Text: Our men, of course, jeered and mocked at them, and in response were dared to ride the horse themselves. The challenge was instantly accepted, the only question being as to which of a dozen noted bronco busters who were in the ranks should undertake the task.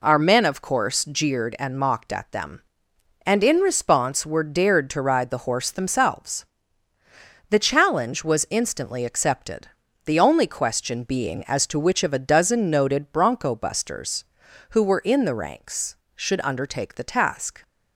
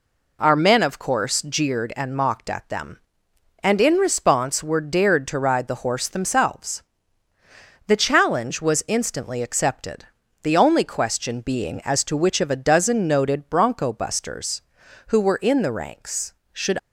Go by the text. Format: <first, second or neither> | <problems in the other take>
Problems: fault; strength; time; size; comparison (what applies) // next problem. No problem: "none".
first | stops before "undertake the task"; at 16.7 s